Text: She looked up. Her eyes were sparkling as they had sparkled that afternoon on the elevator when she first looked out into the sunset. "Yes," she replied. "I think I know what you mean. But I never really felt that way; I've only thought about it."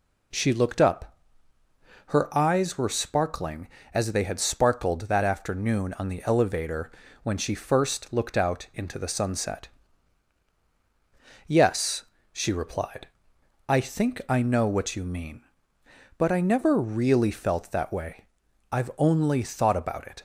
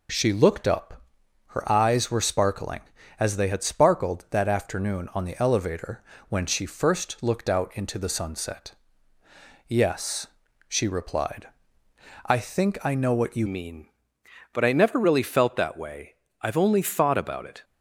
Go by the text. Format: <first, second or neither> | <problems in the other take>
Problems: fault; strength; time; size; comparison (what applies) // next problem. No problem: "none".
first | pauses between "elevator" and "when"; slight; at 6.0 s; 0.26 s long; slight in the first // changes voice at "mean"; from 13.4 s on; 4.2 s long